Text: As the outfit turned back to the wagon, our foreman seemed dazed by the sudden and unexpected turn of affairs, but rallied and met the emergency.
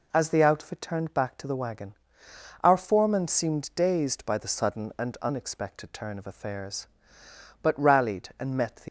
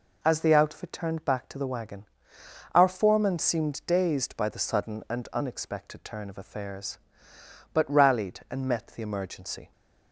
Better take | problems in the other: second | stops before "emergency"; at 8.8 s

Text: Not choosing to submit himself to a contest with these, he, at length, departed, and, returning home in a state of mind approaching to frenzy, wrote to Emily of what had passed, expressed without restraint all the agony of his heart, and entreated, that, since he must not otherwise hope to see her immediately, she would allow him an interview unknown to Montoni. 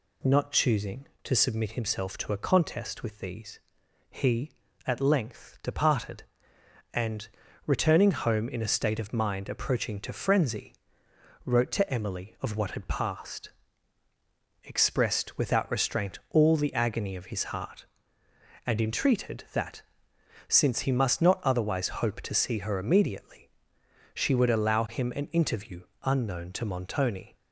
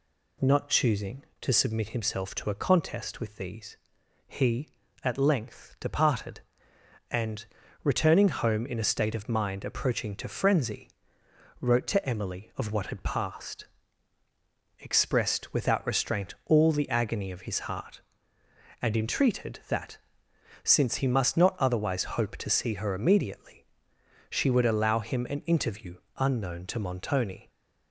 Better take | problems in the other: neither | pauses between "interview" and "unknown"; slight; the same in both

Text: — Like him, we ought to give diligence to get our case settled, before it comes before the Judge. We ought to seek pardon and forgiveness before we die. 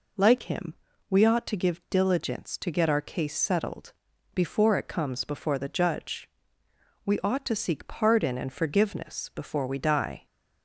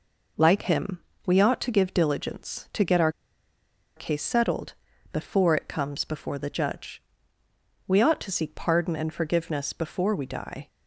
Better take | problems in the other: first | pauses between "our" and "case"; noticeable; at 3.1 s; 0.85 s long

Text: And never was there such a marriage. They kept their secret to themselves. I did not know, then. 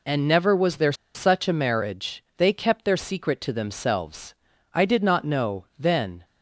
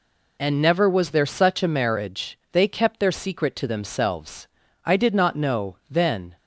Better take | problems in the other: second | pauses between "there" and "such"; slight; at 0.9 s; 0.21 s long

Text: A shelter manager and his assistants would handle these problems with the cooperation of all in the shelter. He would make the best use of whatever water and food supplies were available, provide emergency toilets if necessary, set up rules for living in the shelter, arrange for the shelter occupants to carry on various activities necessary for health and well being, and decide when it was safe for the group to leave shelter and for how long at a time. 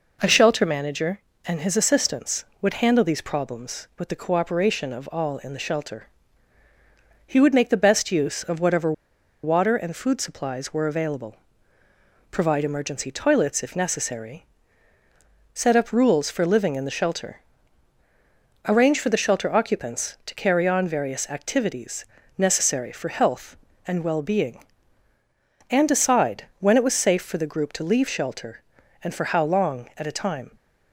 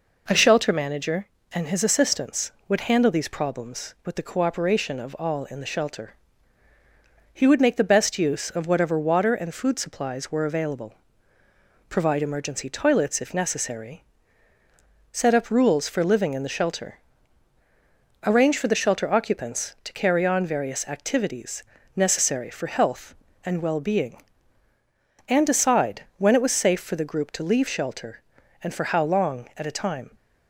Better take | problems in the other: second | pauses between "whatever" and "water"; noticeable; at 8.9 s; 0.51 s long // pauses between "activities" and "necessary"; slight; at 22.0 s; 0.32 s long; slight in the second // pauses between "decide" and "when"; slight; at 26.4 s; 0.16 s long; slight in the second

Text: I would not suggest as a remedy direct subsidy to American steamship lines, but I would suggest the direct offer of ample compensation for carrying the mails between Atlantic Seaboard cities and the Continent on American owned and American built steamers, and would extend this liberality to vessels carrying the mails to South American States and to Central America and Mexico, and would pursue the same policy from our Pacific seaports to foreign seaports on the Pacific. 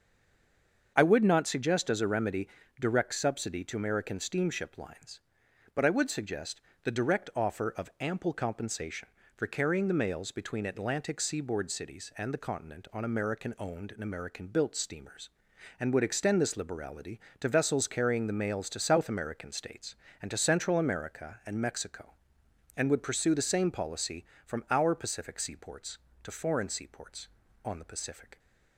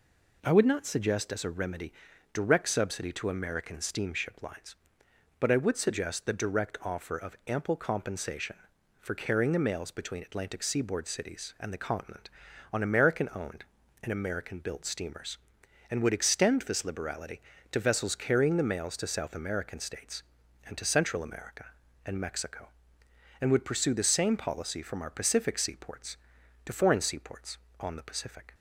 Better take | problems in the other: second | stays silent before the first word; slight; until 0.9 s; 0.9 s long // starts louder than the rest; until 1.9 s; 7 dB // pauses between "remedy" and "direct"; slight; at 2.4 s; 0.32 s long; also in the second // pauses between "suggest" and "the"; slight; at 6.6 s; 0.22 s long

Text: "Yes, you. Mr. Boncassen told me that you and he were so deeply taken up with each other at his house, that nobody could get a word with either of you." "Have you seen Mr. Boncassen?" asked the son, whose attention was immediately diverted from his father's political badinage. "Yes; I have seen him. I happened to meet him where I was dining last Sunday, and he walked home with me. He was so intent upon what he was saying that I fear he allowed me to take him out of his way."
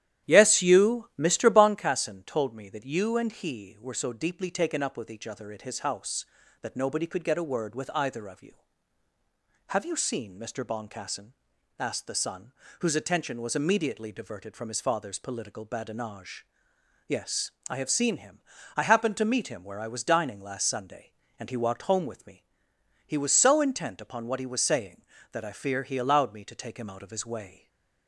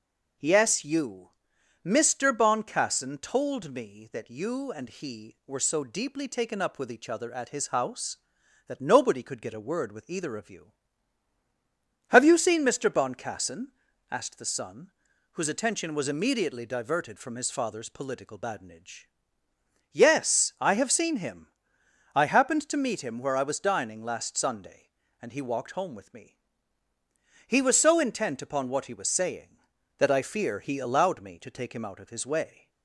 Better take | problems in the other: second | starts louder than the rest; strong; until 1.7 s; 11.5 dB // stays silent after the last word; slight; from 27.4 s on; 0.6 s long

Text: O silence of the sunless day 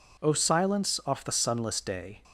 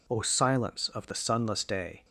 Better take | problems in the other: second | says "off" for "of"; at 1.0 s

